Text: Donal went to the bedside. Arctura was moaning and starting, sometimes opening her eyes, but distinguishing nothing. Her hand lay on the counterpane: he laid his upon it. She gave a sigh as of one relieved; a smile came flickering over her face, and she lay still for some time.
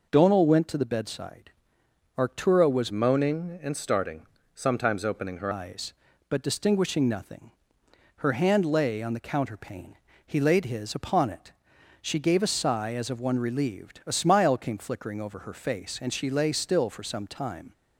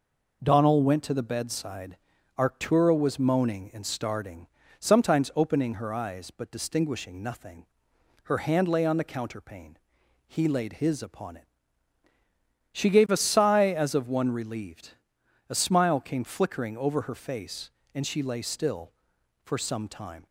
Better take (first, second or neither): second